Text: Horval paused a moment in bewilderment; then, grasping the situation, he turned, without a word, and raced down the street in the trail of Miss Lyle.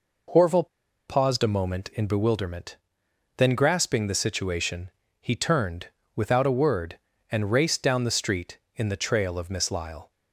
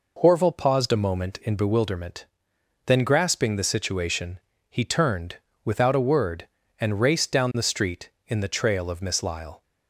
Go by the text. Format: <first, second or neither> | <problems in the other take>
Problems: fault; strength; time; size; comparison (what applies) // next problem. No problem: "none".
second | pauses between "Horval" and "paused"; at 0.6 s; 0.39 s long